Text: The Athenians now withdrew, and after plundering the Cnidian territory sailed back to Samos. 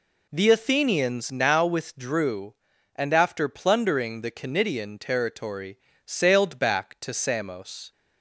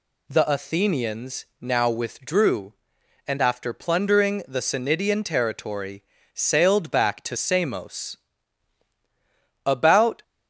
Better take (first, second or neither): first